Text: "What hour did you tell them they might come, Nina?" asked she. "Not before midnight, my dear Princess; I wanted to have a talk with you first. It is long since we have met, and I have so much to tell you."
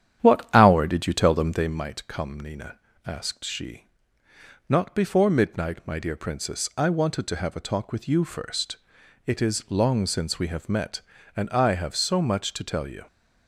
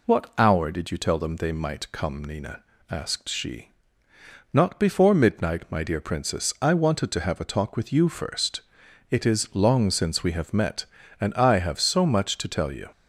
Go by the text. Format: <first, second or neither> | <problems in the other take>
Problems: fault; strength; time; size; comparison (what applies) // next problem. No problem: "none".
second | starts louder than the rest; strong; until 1.9 s; 10 dB